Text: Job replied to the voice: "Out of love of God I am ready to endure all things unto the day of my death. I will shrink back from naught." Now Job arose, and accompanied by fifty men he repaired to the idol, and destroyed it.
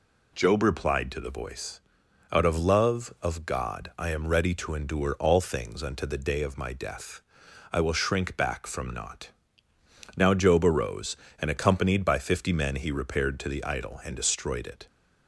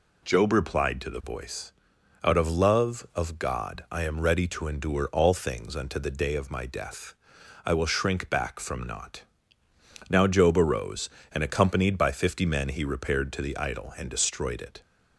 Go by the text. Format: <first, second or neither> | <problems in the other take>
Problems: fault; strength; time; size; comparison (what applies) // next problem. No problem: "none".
neither | none